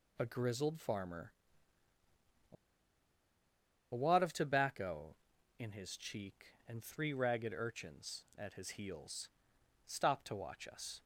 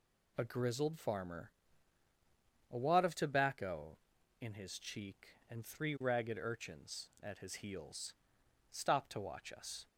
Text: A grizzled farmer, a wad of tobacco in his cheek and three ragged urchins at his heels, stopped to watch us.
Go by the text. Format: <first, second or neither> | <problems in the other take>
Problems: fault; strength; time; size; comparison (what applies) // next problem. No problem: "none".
second | pauses between "a" and "wad"; strong; at 2.5 s; 1.3 s long